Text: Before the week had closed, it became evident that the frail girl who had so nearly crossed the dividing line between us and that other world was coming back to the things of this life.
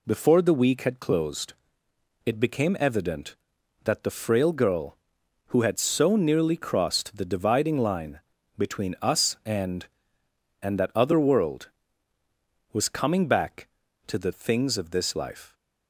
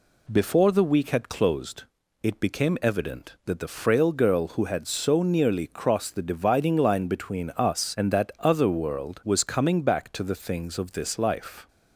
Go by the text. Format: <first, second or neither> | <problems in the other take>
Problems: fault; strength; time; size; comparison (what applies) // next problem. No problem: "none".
second | pauses between "line" and "between"; at 8.1 s; 0.38 s long // says "and" twice; at 10.6 s